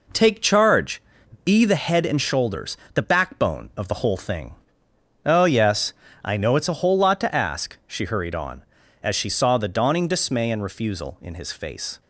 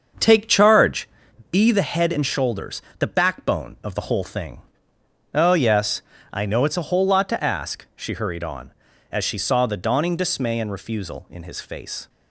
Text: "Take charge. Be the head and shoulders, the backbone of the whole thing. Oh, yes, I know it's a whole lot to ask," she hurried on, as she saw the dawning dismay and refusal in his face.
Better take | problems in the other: first | starts louder than the rest; until 1.3 s; 6.5 dB

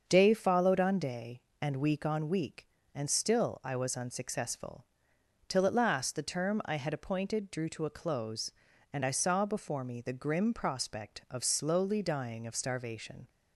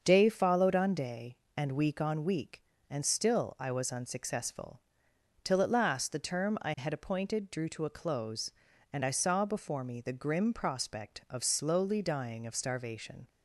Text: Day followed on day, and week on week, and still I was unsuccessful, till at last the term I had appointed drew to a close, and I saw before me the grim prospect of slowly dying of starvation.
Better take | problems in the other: neither | starts louder than the rest; the same in both

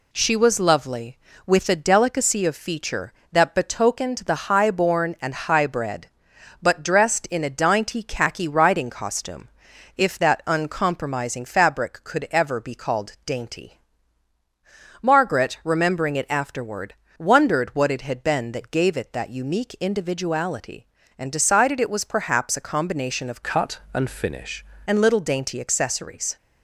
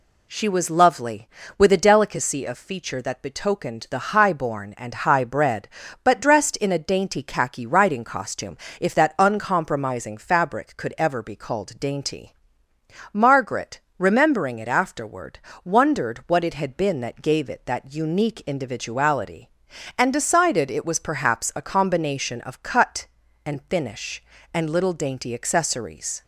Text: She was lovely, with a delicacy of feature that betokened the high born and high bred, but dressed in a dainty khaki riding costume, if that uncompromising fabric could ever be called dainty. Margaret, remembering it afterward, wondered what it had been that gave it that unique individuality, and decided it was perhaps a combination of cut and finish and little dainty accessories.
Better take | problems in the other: second | changes voice from "cut" to "finish"; from 23.4 to 24.6 s; 1.2 s long

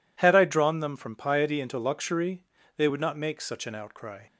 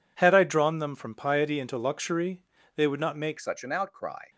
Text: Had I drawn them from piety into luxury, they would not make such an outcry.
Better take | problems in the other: first | changes voice at "such"; from 3.3 s on; 0.9 s long

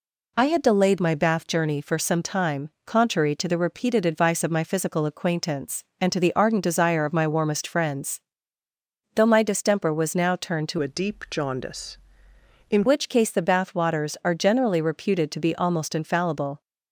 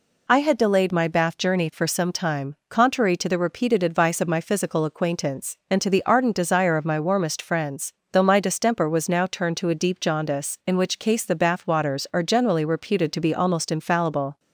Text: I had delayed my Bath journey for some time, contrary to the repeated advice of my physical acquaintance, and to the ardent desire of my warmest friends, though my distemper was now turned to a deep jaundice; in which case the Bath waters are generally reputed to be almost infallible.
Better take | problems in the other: second | changes voice from "a" to "in"; from 10.7 to 12.8 s; 2.1 s long

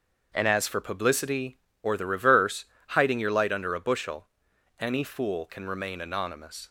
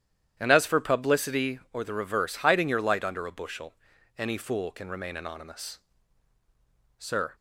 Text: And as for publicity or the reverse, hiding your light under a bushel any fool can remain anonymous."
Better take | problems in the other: first | starts louder than the rest; strong; until 1.3 s; 11 dB; also in the first // pauses between "bushel" and "any"; at 3.7 s; 0.44 s long; noticeable in the first // goes on to say "Sir"; slight; from 6.9 s on; 0.36 s long

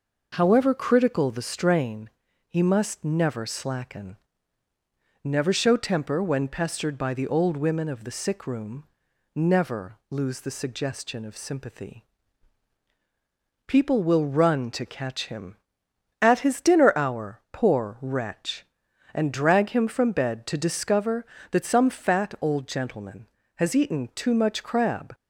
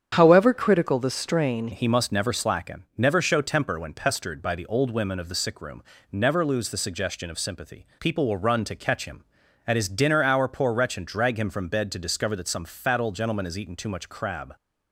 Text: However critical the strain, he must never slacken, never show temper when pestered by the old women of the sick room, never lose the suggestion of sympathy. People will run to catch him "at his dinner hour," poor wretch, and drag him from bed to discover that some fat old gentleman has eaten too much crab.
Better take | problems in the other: first | starts louder than the rest; strong; until 1.2 s; 8 dB // changes voice at "he"; from 1.7 s on; 12.8 s long

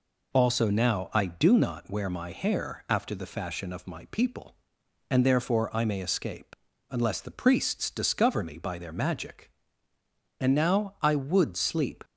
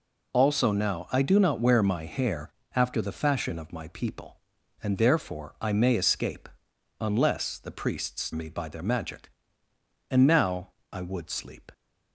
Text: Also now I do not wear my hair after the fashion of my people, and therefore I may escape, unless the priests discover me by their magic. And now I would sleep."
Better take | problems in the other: first | pauses between "hair" and "after"; slight; at 2.5 s; 0.24 s long // skips "discover"; at 8.3 s // pauses between "now" and "I"; slight; at 10.7 s; 0.20 s long

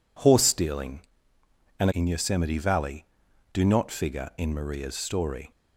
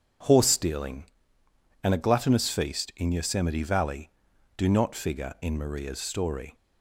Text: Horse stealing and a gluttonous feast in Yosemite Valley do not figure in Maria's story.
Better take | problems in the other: second | skips "a gluttonous feast"; at 1.9 s

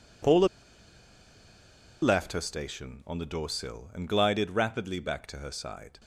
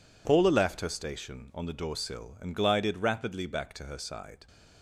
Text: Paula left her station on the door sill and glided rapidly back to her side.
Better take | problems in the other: second | pauses between "Paula" and "left"; strong; at 0.4 s; 1.5 s long

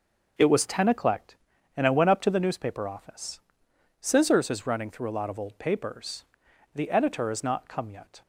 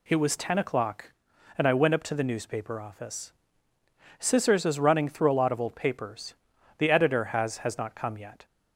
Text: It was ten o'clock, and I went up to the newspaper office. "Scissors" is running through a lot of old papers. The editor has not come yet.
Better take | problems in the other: first | says "has" twice; at 7.5 s

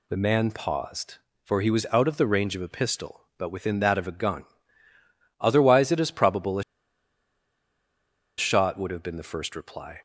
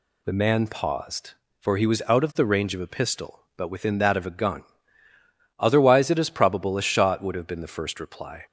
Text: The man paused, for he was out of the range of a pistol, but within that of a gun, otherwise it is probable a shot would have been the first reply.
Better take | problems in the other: second | pauses between "a" and "shot"; strong; at 6.6 s; 1.7 s long

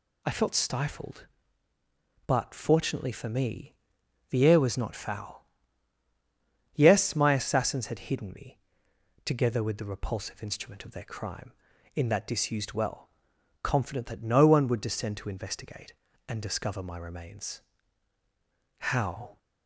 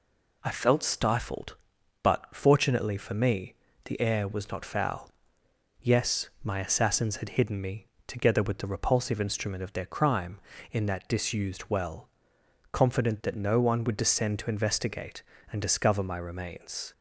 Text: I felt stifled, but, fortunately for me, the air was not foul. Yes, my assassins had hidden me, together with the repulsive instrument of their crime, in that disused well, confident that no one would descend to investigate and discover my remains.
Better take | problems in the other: second | goes on to say "How"; from 18.7 s on; 0.60 s long

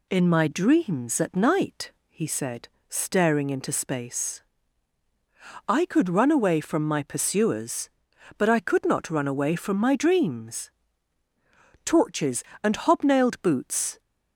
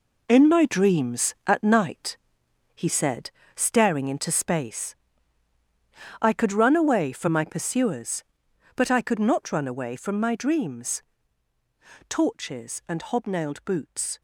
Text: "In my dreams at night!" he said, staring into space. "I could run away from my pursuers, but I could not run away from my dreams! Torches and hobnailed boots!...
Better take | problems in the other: first | gets quieter; strong; throughout; 9.5 dB

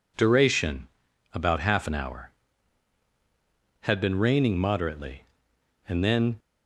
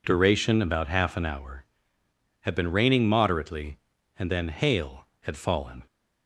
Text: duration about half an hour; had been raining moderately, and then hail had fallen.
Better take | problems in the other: second | pauses between "duration" and "about"; noticeable; at 0.8 s; 0.46 s long // stops before "hail had fallen"; at 6.3 s

